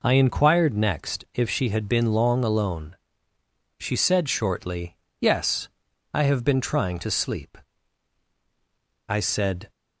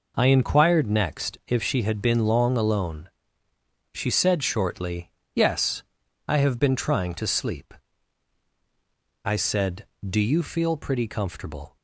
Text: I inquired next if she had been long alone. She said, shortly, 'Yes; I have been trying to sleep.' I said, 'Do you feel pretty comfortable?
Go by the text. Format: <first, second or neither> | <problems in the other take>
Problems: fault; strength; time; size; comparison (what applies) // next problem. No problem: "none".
second | stops before "Do you feel pretty comfortable"; at 9.6 s